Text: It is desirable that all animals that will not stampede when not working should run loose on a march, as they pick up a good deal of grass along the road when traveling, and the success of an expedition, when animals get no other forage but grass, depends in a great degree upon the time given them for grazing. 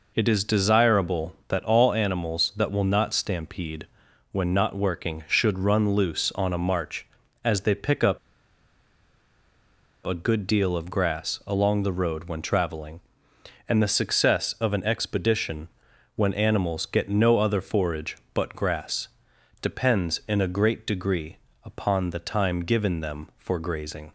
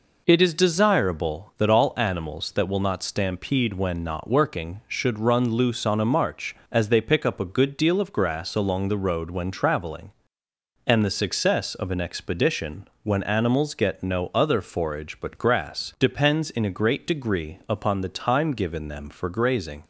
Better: second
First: pauses between "stampede" and "when"; at 3.8 s; 0.44 s long // pauses between "up" and "a"; strong; at 8.1 s; 1.8 s long // pauses between "degree" and "upon"; slight; at 21.3 s; 0.30 s long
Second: none

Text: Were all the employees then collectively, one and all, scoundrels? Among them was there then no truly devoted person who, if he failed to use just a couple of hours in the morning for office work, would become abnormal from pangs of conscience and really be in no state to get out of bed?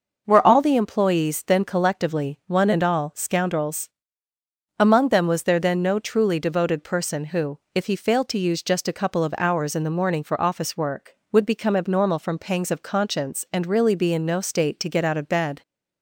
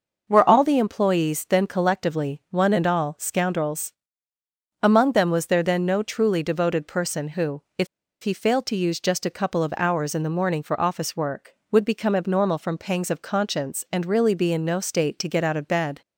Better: first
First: none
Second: starts louder than the rest; noticeable; until 1.2 s; 6 dB // pauses between "if" and "he"; at 7.8 s; 0.36 s long

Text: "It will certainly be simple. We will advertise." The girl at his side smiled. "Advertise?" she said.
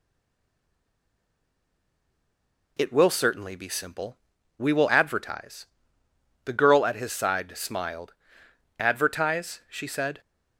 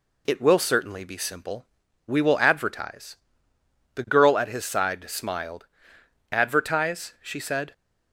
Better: second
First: stays silent before the first word; strong; until 2.7 s; 2.7 s long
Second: none

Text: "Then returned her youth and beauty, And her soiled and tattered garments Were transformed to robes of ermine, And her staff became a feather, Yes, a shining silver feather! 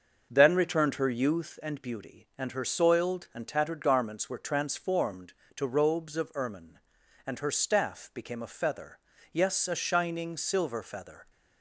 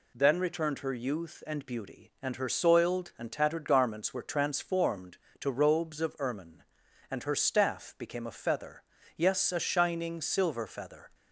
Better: second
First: starts louder than the rest; until 1.6 s; 6 dB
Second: none

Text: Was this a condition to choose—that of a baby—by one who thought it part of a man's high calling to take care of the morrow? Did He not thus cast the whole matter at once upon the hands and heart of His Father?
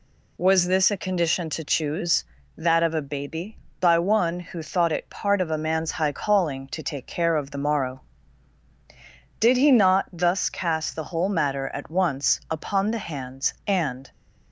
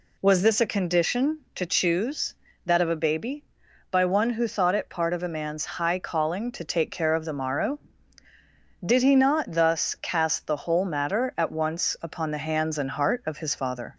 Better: second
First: stops before "heart of His Father"; at 14.1 s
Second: none

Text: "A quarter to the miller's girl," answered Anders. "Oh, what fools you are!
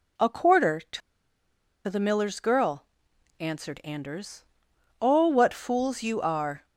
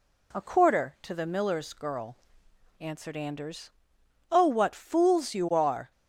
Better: second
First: pauses between "to" and "the"; noticeable; at 1.0 s; 0.87 s long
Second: none

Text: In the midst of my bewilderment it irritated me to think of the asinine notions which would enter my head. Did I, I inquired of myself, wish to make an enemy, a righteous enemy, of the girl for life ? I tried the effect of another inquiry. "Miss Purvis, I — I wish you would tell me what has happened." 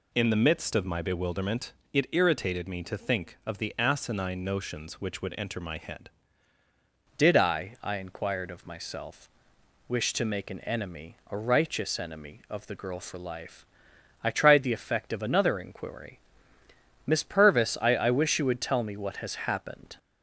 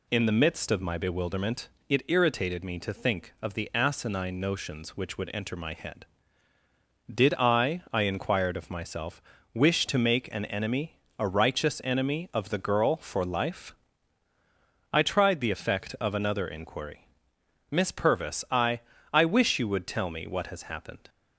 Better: second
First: pauses between "bewilderment" and "it"; slight; at 1.7 s; 0.22 s long // changes voice at "Did"; from 7.1 s on; 12.8 s long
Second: pauses between "bewilderment" and "it"; slight; at 1.6 s; 0.22 s long

